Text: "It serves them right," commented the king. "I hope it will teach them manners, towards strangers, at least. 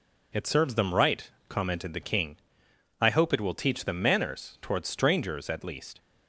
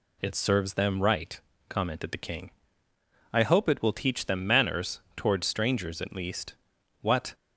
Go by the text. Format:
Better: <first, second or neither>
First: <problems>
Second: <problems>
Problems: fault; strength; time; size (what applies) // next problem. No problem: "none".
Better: first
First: none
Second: goes on to say "What"; slight; from 7.0 s on; 0.32 s long